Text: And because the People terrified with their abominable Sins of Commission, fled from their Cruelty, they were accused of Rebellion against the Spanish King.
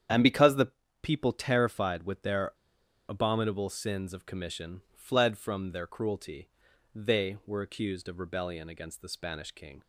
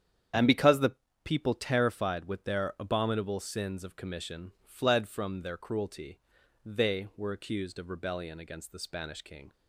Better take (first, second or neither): second